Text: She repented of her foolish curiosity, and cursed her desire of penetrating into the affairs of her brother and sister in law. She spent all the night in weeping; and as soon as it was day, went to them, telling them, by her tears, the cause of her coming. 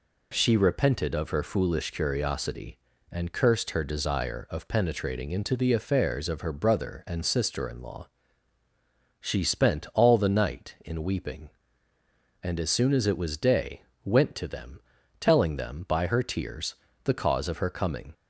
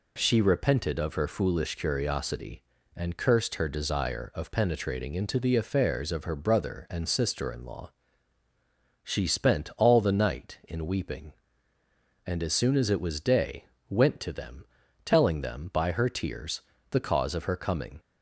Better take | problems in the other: neither | none

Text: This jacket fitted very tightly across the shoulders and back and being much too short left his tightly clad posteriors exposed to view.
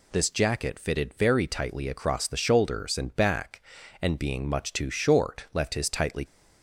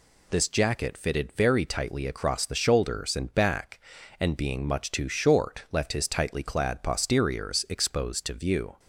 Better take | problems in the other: second | stops before "clad posteriors exposed to view"; at 6.2 s

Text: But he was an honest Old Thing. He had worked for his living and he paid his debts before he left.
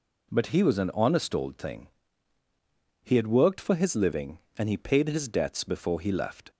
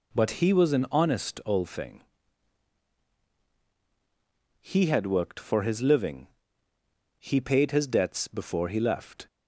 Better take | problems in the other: first | skips "and"; at 6.7 s

